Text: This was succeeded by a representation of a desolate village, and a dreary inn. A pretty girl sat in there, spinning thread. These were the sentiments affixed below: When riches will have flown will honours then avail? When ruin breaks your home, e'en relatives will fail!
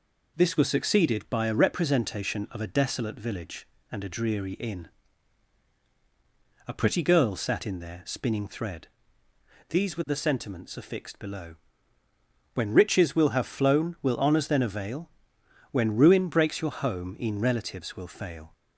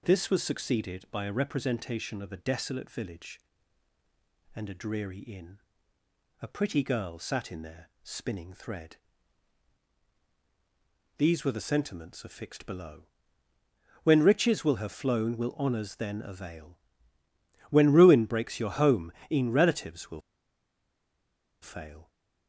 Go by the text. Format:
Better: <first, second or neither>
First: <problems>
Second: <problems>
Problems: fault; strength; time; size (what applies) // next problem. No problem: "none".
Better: first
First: none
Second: pauses between "will" and "fail"; strong; at 20.2 s; 1.4 s long